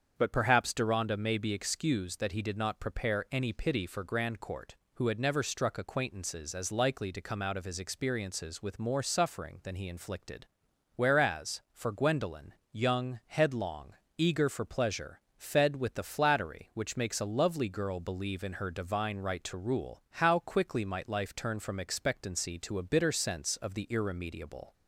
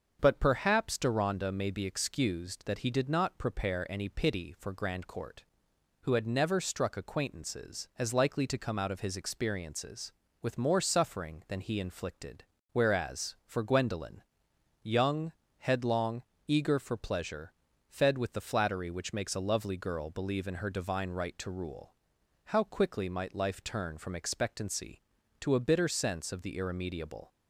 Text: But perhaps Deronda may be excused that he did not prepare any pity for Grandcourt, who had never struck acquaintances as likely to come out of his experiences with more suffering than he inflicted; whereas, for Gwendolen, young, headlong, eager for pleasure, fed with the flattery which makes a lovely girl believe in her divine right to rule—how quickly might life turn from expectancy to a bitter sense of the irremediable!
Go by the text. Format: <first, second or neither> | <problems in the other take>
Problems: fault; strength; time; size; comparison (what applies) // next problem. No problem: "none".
neither | starts louder than the rest; the same in both